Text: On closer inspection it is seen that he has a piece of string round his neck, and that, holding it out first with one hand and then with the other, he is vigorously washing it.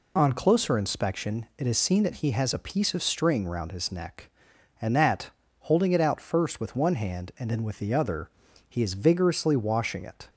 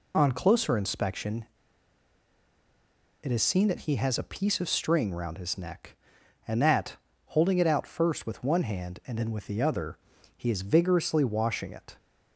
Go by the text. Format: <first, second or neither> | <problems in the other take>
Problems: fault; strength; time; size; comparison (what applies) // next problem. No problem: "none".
first | pauses between "inspection" and "it"; strong; at 1.4 s; 1.7 s long